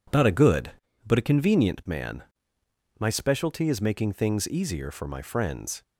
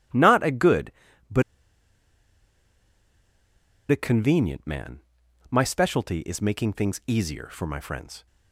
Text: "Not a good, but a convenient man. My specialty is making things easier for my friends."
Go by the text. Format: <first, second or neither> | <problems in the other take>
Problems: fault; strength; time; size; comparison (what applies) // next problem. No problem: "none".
first | pauses between "but" and "a"; strong; at 1.4 s; 2.4 s long